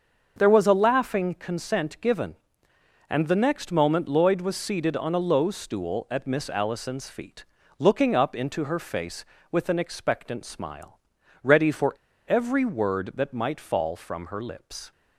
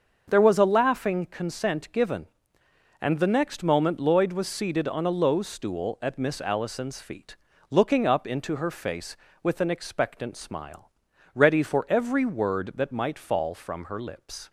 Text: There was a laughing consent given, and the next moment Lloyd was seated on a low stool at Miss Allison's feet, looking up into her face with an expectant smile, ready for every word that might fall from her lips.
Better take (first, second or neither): second